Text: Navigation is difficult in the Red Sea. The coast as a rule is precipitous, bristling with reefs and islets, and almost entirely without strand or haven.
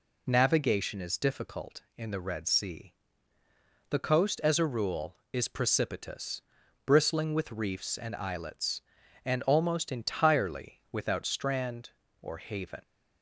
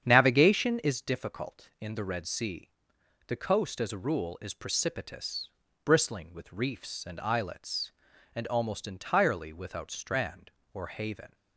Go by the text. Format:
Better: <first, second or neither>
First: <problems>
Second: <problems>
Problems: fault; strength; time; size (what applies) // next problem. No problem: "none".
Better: first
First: none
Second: starts louder than the rest; strong; until 1.0 s; 8.5 dB